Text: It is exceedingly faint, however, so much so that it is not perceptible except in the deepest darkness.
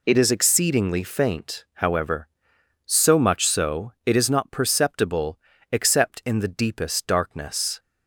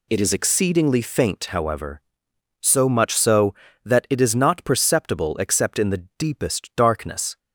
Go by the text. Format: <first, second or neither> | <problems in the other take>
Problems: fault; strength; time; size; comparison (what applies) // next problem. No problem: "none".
second | skips "that"; at 3.9 s // pauses between "perceptible" and "except"; slight; at 5.3 s; 0.32 s long